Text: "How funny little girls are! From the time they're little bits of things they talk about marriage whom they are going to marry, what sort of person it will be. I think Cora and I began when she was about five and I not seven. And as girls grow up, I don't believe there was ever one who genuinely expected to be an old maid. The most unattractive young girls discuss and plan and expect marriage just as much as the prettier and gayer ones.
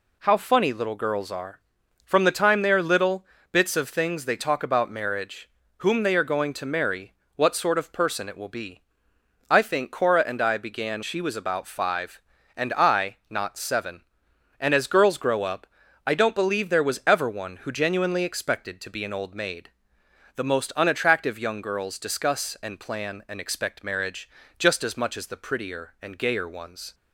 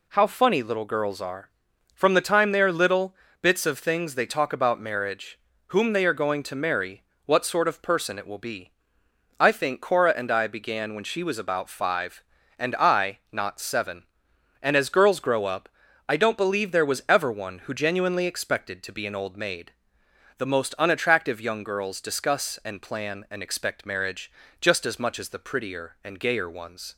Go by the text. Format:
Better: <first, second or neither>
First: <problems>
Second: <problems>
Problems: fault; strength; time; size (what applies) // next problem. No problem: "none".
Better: second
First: pauses between "little" and "bits"; slight; at 3.2 s; 0.28 s long // pauses between "marriage" and "whom"; slight; at 5.4 s; 0.30 s long // skips "when"; at 11.0 s // pauses between "marriage" and "just"; slight; at 24.2 s; 0.30 s long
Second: pauses between "little" and "bits"; slight; at 3.1 s; 0.28 s long // pauses between "marriage" and "whom"; slight; at 5.3 s; 0.30 s long // pauses between "marriage" and "just"; slight; at 24.3 s; 0.30 s long